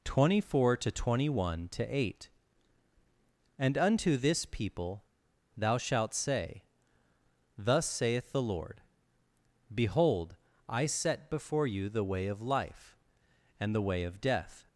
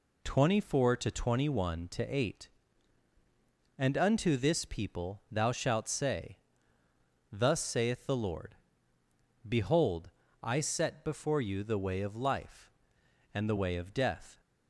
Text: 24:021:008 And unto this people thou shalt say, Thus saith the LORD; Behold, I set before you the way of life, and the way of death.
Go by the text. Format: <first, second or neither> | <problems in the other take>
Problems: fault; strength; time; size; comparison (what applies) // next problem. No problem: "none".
second | pauses between "people" and "thou"; noticeable; at 5.0 s; 0.53 s long